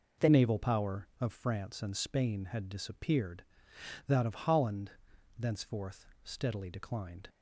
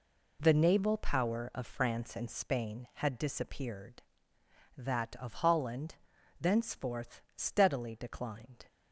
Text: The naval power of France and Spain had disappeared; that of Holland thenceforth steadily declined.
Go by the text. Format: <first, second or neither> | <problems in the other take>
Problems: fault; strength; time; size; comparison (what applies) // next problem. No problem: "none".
second | changes voice at "naval"; from 0.3 s on; 6.9 s long // pauses between "Holland" and "thenceforth"; noticeable; at 4.9 s; 0.46 s long; also in the second // pauses between "thenceforth" and "steadily"; slight; at 6.0 s; 0.18 s long; slight in the second